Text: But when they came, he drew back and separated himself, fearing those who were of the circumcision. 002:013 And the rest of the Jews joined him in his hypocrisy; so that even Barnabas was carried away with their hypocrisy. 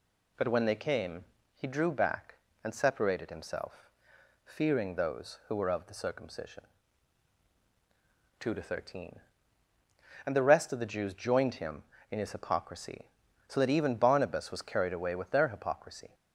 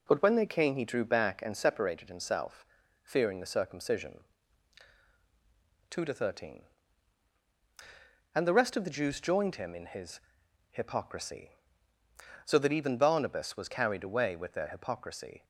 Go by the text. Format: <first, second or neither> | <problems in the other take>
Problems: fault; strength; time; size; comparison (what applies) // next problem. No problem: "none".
first | skips "those who were of"; at 3.4 s // pauses between "his" and "hypocrisy"; noticeable; at 10.1 s; 0.52 s long